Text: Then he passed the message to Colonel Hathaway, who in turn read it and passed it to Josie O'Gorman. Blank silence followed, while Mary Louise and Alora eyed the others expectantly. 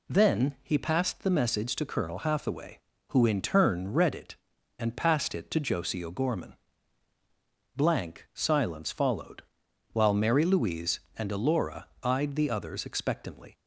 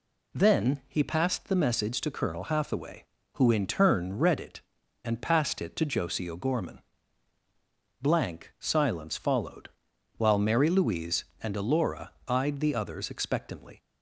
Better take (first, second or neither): neither